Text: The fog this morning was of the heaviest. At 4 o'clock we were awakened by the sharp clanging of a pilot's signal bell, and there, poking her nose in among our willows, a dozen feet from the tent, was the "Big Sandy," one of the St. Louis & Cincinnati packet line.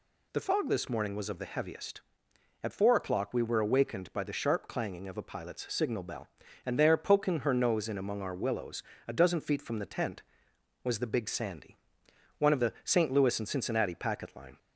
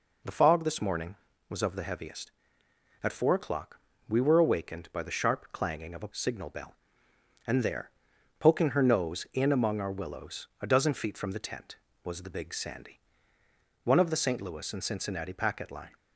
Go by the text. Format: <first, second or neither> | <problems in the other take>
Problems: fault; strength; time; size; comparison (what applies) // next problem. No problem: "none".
first | pauses between "o'clock" and "we"; slight; at 3.7 s; 0.26 s long // skips "pilot's"; at 6.1 s